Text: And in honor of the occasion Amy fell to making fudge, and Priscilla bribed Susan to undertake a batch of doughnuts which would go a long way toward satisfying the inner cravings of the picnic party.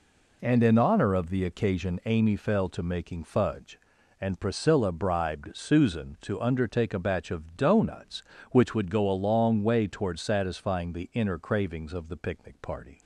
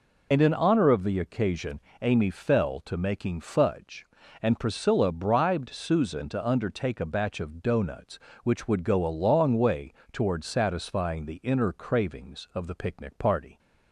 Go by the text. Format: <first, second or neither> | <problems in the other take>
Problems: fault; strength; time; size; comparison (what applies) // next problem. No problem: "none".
first | loses the start of "And"; at 0.3 s; 45 ms // pauses between "occasion" and "Amy"; slight; at 1.8 s; 0.20 s long // pauses between "way" and "toward"; slight; at 9.9 s; 0.20 s long